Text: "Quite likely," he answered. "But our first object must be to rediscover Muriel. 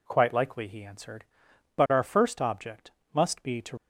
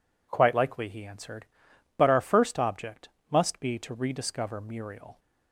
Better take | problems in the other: second | pauses between "object" and "must"; slight; at 2.9 s; 0.22 s long; slight in the second // stops before "rediscover Muriel"; at 3.7 s

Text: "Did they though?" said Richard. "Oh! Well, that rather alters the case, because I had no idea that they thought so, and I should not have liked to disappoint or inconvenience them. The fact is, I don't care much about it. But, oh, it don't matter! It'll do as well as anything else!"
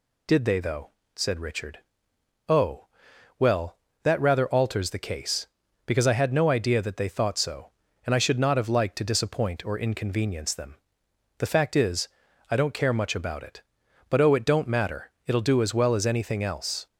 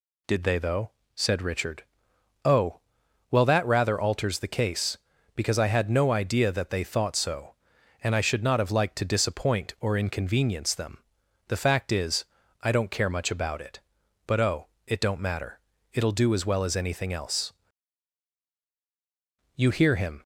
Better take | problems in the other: first | goes on to say "You hear him"; noticeable; from 19.5 s on; 0.66 s long

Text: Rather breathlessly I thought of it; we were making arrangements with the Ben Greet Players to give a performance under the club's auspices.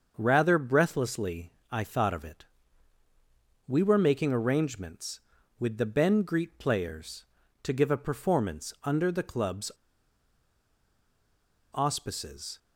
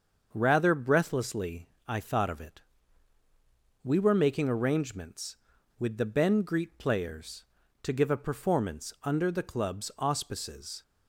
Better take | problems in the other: second | starts louder than the rest; until 1.1 s; 6.5 dB; also in the second // pauses between "breathlessly" and "I"; slight; at 1.5 s; 0.22 s long; slight in the second // pauses between "club's" and "auspices"; strong; at 9.7 s; 1.9 s long

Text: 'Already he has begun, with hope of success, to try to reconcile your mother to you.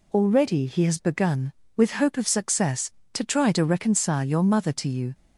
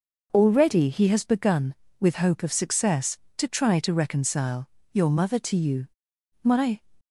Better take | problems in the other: first | pauses between "reconcile" and "your"; slight; at 4.6 s; 0.24 s long // goes on to say "My"; slight; from 6.4 s on; 0.38 s long

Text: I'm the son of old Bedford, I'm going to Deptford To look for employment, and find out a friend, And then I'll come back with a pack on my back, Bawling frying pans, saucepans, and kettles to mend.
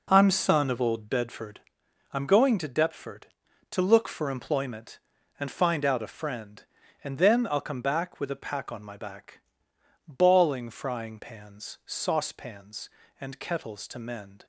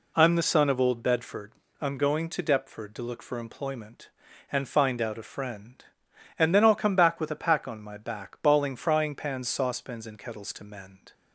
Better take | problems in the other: second | skips "the"; at 0.3 s

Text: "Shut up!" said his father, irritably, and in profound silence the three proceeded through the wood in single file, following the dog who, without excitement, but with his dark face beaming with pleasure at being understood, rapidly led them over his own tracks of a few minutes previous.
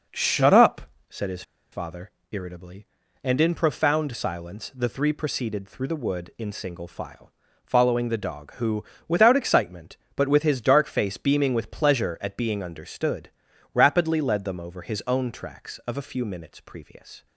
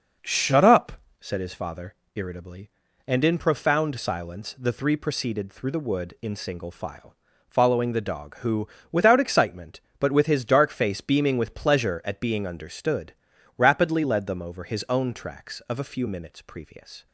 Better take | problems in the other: second | pauses between "his" and "father"; slight; at 1.4 s; 0.29 s long

